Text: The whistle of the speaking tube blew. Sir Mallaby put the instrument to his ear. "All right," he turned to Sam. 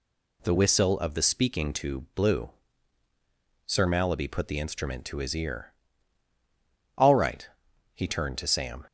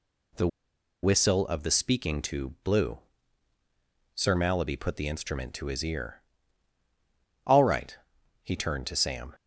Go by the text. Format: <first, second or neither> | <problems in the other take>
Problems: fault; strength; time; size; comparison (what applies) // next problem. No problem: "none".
first | pauses between "The" and "whistle"; noticeable; at 0.4 s; 0.55 s long